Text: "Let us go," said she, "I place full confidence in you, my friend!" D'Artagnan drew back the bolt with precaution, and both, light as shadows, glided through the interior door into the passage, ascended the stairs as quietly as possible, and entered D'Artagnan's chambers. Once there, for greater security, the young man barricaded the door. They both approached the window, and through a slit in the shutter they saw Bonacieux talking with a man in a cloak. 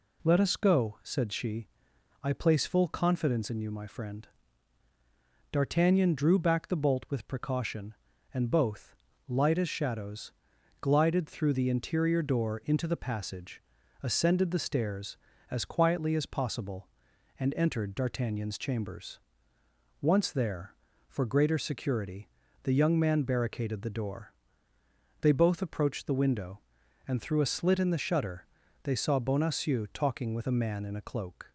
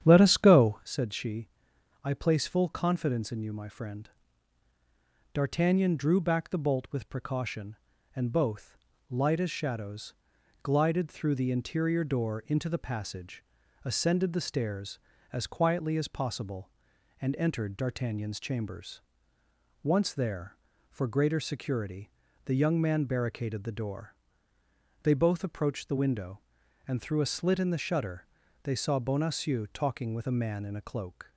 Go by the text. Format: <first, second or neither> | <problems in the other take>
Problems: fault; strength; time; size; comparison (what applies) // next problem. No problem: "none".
first | starts louder than the rest; strong; until 0.9 s; 9.5 dB // pauses between "shutter" and "they"; at 28.2 s; 0.38 s long; also in the first